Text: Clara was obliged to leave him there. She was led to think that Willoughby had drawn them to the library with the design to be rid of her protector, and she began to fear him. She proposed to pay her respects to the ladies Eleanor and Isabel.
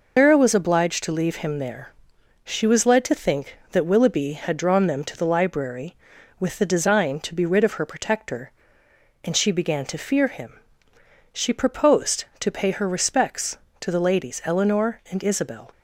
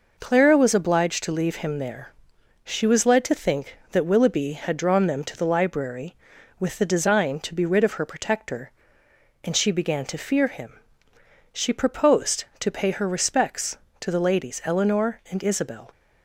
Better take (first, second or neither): second